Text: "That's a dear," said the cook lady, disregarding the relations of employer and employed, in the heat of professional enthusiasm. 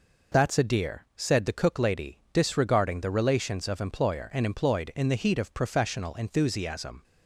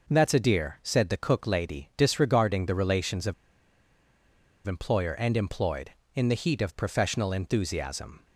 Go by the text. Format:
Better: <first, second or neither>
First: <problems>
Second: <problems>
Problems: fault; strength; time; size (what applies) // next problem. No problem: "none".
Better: first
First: none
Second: pauses between "of" and "employer"; strong; at 3.3 s; 1.3 s long